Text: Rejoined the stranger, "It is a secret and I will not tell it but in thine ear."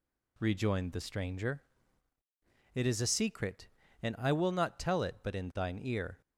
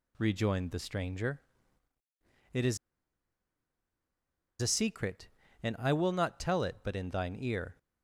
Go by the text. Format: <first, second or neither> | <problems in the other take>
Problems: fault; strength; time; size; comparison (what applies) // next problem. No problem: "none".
first | pauses between "is" and "a"; strong; at 2.7 s; 1.8 s long